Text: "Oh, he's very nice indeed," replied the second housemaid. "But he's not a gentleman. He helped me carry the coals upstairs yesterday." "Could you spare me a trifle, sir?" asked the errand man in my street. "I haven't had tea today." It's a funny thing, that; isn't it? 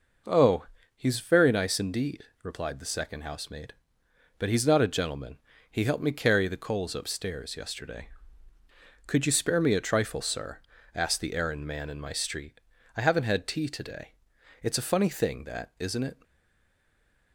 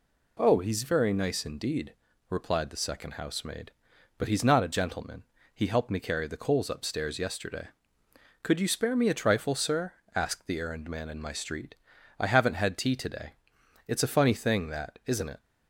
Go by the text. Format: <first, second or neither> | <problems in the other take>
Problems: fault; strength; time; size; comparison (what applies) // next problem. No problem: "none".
second | stays silent after the last word; from 16.2 s on; 1.1 s long